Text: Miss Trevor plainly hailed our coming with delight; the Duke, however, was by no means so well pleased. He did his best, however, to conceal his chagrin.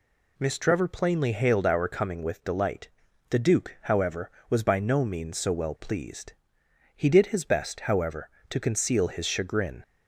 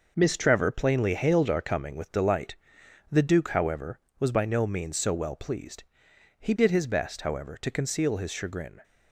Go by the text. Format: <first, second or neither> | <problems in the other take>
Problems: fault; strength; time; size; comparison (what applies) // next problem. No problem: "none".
first | gets quieter; strong; throughout; 7.5 dB